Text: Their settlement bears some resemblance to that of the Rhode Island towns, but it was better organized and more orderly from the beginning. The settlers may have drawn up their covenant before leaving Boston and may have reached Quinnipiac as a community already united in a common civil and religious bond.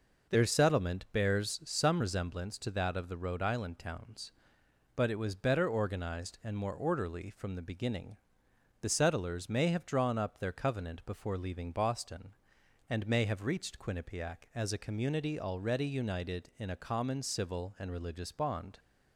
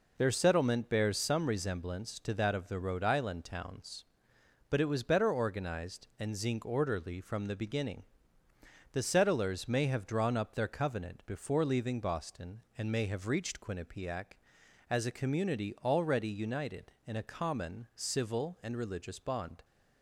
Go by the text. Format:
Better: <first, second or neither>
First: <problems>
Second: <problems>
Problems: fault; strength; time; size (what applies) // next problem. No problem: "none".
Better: first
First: none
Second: says "zinc" for "more"; at 6.3 s